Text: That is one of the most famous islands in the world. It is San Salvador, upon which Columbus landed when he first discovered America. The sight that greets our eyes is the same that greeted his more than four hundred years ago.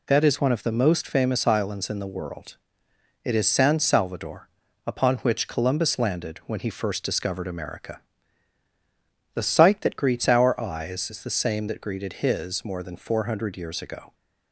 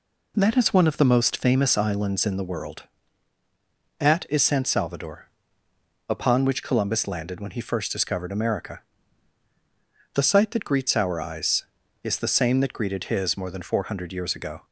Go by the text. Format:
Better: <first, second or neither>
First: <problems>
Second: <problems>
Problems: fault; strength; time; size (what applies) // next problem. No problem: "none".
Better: first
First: none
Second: says "At" for "It"; at 4.0 s